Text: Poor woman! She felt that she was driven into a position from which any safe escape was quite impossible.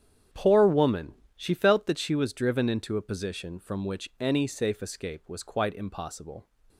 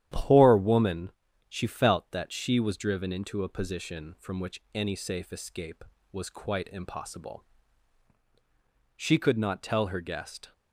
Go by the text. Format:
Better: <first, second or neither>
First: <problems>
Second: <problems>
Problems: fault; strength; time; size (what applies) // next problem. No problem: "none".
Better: first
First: starts louder than the rest; strong; until 1.5 s; 9 dB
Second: starts louder than the rest; strong; until 1.5 s; 11 dB // goes on to say "She could not tell her guest"; from 8.9 s on; 1.5 s long